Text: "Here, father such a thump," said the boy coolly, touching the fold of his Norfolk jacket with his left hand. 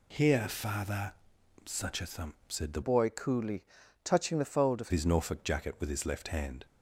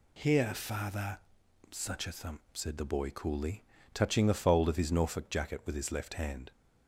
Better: second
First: pauses between "father" and "such"; noticeable; at 1.1 s; 0.50 s long // changes voice from "boy" to "of"; from 2.8 to 4.9 s; 2.1 s long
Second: pauses between "father" and "such"; noticeable; at 1.1 s; 0.50 s long

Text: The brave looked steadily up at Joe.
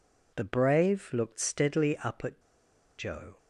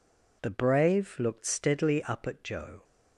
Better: second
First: pauses between "at" and "Joe"; noticeable; at 2.4 s; 0.57 s long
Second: none

